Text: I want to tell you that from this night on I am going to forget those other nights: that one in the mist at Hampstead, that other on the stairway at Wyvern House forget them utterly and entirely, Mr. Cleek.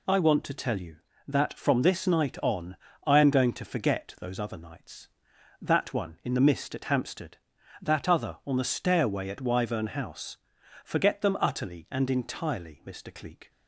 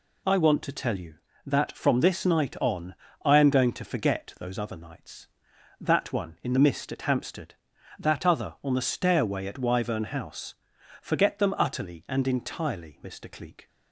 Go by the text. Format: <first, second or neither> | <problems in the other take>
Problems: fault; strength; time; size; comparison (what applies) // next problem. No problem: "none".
neither | pauses between "on" and "I"; slight; the same in both // pauses between "House" and "forget"; noticeable; the same in both